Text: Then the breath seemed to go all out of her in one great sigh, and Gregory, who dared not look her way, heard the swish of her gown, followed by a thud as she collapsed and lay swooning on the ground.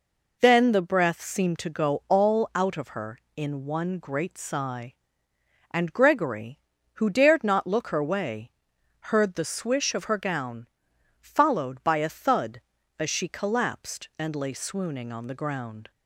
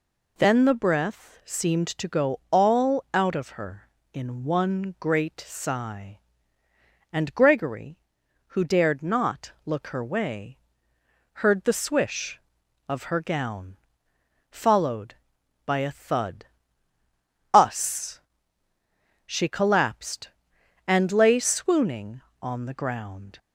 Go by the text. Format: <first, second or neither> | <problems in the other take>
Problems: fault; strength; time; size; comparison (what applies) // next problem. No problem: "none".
first | says "us" for "as"; at 17.5 s